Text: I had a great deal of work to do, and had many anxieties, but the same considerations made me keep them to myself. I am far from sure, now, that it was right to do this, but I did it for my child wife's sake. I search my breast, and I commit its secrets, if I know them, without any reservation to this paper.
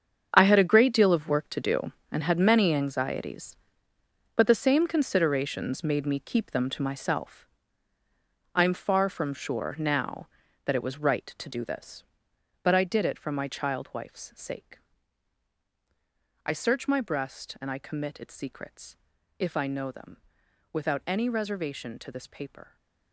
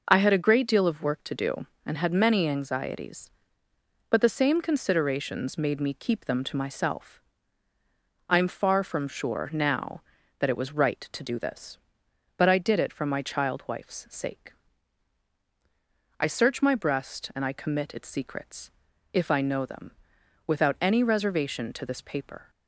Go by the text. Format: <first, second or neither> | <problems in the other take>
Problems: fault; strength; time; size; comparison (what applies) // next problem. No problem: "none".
second | gets quieter; strong; throughout; 12 dB